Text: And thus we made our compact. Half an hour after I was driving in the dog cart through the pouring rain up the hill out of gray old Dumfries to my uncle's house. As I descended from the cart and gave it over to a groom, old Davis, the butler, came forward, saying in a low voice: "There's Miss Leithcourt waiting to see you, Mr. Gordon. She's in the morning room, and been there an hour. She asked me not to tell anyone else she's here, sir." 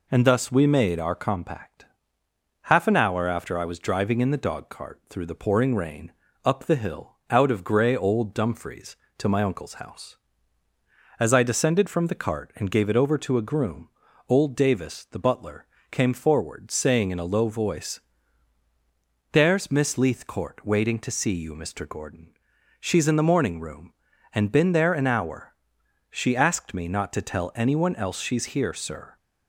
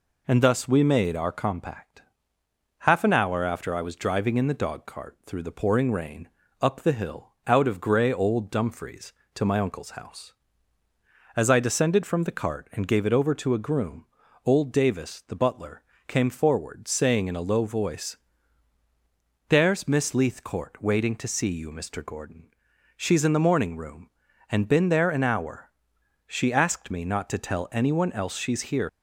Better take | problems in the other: first | pauses between "rain" and "up"; slight; at 6.2 s; 0.32 s long; slight in the first // stops before "sir"; at 28.8 s

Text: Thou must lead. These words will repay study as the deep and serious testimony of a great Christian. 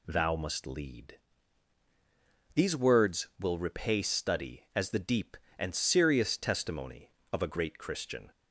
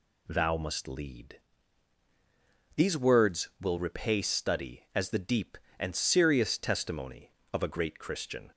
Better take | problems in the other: neither | none

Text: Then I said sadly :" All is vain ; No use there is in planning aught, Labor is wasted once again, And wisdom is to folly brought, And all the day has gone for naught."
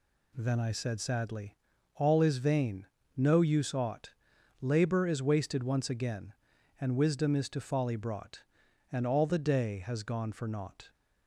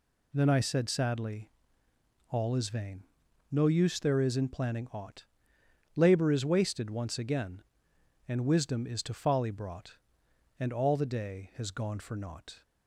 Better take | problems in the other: second | skips "there is in planning"; at 3.7 s

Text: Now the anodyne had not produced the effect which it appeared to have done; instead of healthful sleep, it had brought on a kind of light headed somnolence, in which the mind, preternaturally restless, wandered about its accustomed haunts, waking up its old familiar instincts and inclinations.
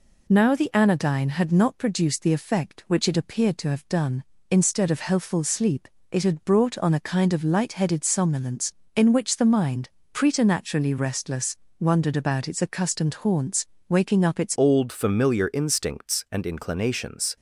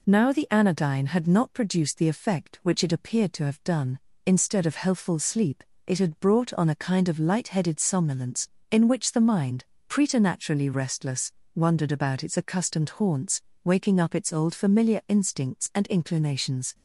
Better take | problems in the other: second | changes voice at "old"; from 14.5 s on; 2.8 s long

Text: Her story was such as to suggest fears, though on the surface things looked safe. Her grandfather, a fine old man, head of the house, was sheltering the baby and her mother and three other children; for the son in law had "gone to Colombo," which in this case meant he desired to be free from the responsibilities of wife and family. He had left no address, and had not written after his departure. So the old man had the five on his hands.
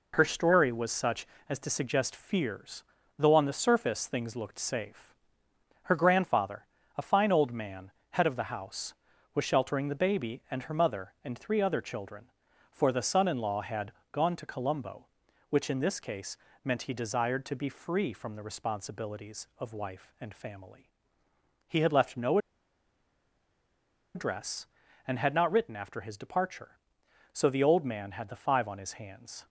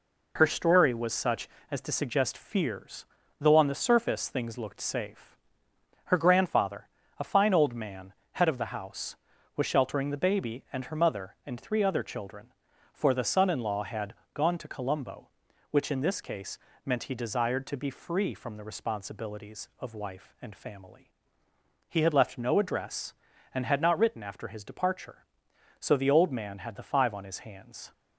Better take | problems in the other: second | pauses between "had" and "gone"; slight; at 13.9 s; 0.22 s long; slight in the second // pauses between "case" and "meant"; slight; at 16.3 s; 0.26 s long; slight in the second // pauses between "no" and "address"; strong; at 22.3 s; 1.7 s long

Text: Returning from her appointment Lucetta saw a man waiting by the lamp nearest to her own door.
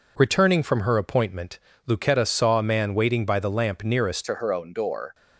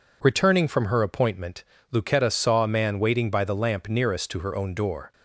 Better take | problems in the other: second | pauses between "appointment" and "Lucetta"; slight; at 1.5 s; 0.28 s long; slight in the second // changes voice at "to"; from 4.2 s on; 0.9 s long

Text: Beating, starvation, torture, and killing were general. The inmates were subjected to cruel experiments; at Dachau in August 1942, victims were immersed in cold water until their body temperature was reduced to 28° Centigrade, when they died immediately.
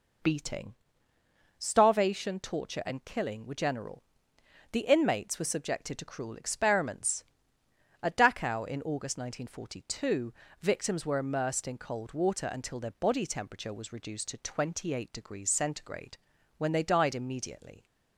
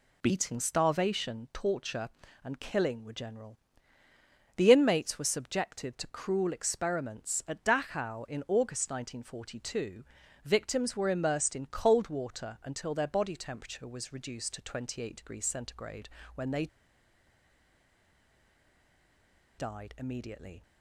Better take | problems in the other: first | pauses between "they" and "died"; strong; at 16.6 s; 2.9 s long

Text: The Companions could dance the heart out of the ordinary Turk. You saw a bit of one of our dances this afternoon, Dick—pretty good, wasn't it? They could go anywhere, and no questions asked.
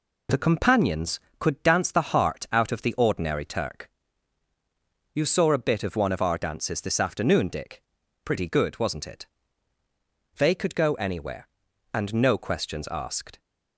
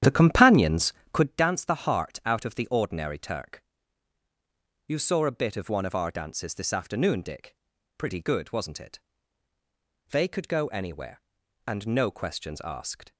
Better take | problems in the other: first | starts louder than the rest; strong; until 1.4 s; 10.5 dB

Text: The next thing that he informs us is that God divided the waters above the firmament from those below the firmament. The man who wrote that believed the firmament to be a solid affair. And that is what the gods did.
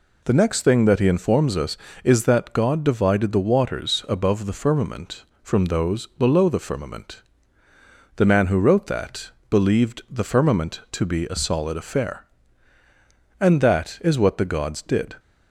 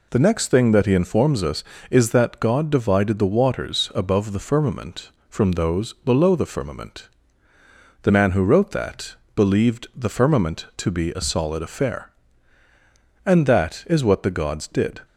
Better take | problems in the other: neither | pauses between "that" and "believed"; slight; the same in both

